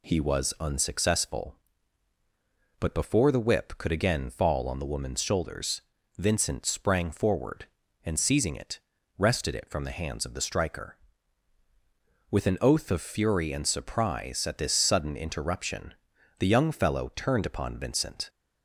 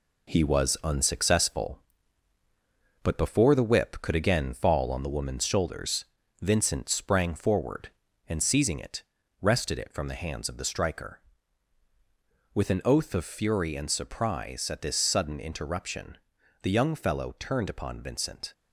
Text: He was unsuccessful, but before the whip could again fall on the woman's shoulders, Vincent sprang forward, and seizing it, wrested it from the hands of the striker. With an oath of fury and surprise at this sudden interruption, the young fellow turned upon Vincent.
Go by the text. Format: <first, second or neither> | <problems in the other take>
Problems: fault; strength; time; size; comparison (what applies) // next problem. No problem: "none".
first | gets quieter; throughout; 6 dB